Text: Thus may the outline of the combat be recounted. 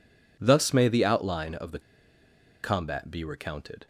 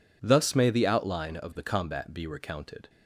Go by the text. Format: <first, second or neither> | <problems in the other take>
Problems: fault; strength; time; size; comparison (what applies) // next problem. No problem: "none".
second | pauses between "the" and "combat"; noticeable; at 1.7 s; 0.83 s long